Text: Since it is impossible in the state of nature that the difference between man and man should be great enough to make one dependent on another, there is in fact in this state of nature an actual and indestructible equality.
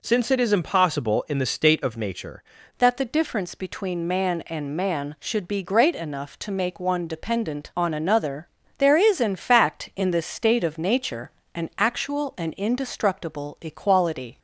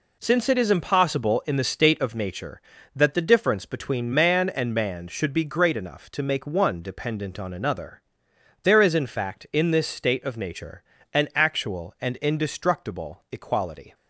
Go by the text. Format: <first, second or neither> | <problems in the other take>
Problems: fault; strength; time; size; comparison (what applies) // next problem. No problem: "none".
second | changes voice at "that"; from 2.7 s on; 11.6 s long // pauses between "nature" and "an"; slight; at 11.3 s; 0.24 s long; slight in the second